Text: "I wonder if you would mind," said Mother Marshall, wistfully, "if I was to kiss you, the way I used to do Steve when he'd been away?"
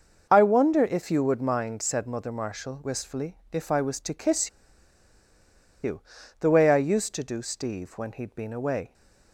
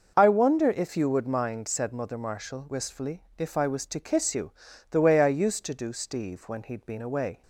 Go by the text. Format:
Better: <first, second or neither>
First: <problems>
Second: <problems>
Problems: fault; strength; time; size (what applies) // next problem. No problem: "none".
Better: second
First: starts louder than the rest; noticeable; until 1.3 s; 6 dB // pauses between "kiss" and "you"; strong; at 4.4 s; 1.3 s long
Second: starts louder than the rest; noticeable; until 1.1 s; 6 dB